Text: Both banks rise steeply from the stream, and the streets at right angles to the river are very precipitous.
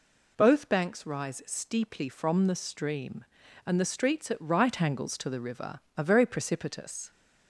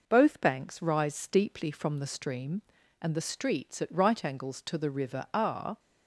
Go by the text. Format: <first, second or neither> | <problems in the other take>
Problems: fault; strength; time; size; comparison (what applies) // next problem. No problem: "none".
first | stops before "very precipitous"; at 5.7 s